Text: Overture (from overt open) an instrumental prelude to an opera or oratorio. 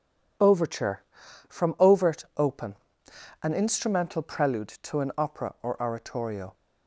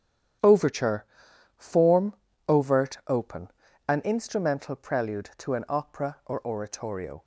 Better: first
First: none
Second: starts louder than the rest; strong; until 1.9 s; 9.5 dB // says "form" for "from"; at 1.5 s

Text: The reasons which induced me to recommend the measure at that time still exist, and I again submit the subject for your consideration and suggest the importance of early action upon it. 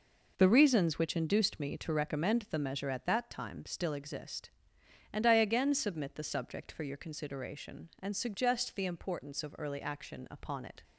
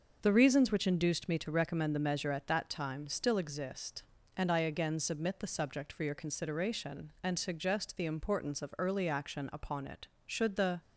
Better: first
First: none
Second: starts louder than the rest; noticeable; until 1.2 s; 6 dB // goes on to say "Should the"; from 10.2 s on; 0.54 s long

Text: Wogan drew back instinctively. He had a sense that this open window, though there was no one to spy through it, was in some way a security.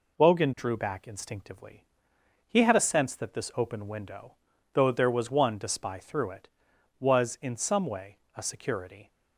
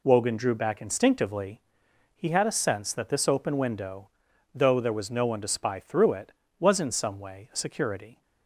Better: second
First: skips "no"; at 5.3 s // pauses between "way" and "a"; slight; at 8.1 s; 0.18 s long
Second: none

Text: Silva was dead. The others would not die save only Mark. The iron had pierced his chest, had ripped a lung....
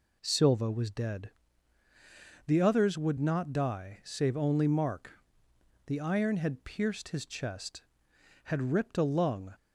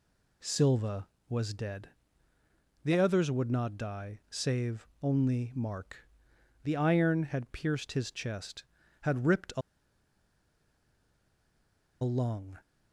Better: first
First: none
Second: pauses between "a" and "lung"; strong; at 9.6 s; 2.4 s long

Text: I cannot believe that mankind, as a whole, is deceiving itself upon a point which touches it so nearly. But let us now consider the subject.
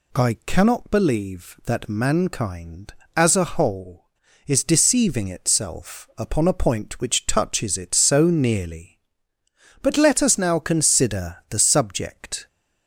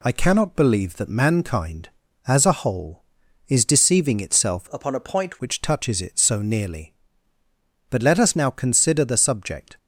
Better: first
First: none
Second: changes voice from "upon" to "point"; from 4.7 to 5.3 s; 0.6 s long

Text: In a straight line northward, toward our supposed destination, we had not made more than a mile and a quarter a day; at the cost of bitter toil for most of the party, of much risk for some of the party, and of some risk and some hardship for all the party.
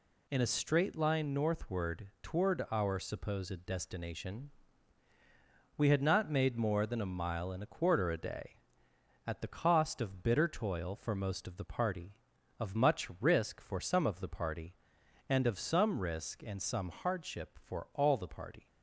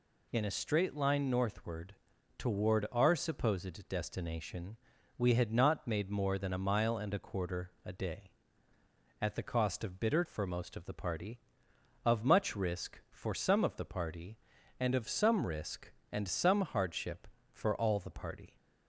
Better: first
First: none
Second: skips "toil"; at 10.2 s

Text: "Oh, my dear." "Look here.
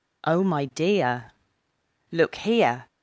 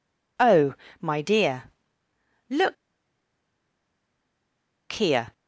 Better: first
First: none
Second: pauses between "Look" and "here"; strong; at 2.7 s; 2.1 s long

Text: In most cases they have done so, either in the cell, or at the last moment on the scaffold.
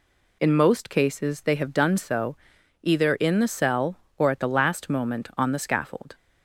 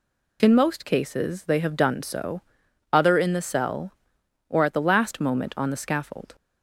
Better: first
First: none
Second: says "other" for "either"; at 2.9 s

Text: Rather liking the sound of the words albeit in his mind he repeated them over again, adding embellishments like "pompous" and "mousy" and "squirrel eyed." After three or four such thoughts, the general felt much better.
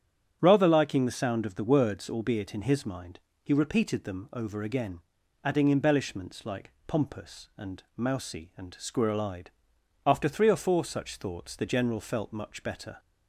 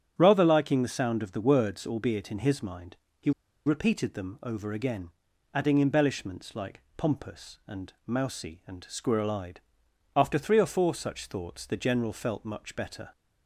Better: first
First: starts louder than the rest; strong; until 1.4 s; 8 dB // pauses between "mind" and "he"; slight; at 3.1 s; 0.24 s long // pauses between "like" and "pompous"; slight; at 6.7 s; 0.16 s long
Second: starts louder than the rest; strong; until 1.1 s; 8 dB // pauses between "mind" and "he"; slight; at 2.9 s; 0.24 s long // pauses between "he" and "repeated"; slight; at 3.3 s; 0.35 s long // pauses between "like" and "pompous"; slight; at 6.8 s; 0.16 s long

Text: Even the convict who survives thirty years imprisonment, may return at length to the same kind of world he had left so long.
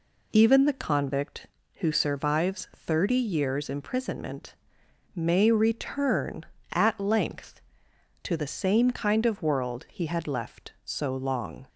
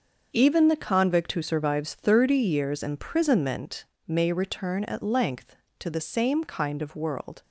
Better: first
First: none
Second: starts louder than the rest; until 1.3 s; 6.5 dB // stops before "he had left so long"; at 7.4 s

